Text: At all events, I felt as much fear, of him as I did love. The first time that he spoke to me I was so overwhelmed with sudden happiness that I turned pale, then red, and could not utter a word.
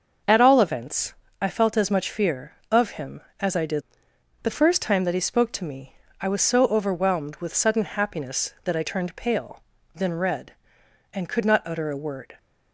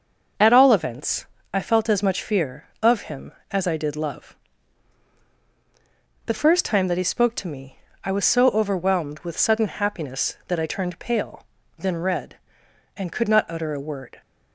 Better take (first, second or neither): second